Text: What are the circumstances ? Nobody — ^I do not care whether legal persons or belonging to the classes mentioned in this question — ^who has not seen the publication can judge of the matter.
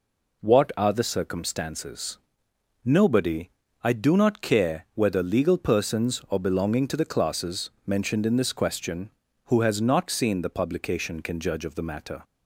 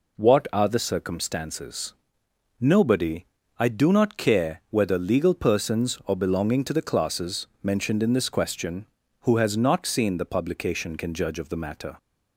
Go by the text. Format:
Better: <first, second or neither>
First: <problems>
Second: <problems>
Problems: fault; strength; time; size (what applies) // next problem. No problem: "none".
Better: neither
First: none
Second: none